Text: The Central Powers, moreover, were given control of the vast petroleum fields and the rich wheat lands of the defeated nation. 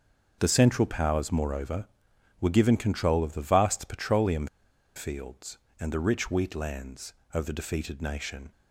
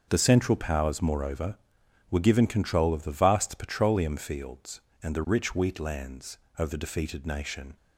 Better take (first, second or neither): second